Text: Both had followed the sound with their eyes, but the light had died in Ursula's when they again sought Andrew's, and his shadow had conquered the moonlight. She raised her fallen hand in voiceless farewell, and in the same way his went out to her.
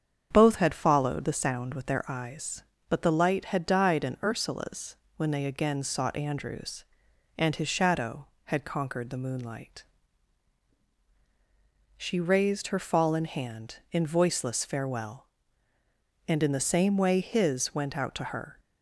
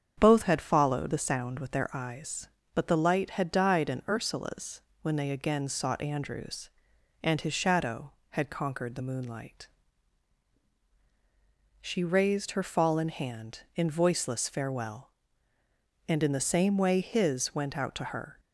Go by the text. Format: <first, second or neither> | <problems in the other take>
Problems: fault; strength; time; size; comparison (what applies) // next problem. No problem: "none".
neither | starts louder than the rest; strong; the same in both // pauses between "Ursula's" and "when"; slight; the same in both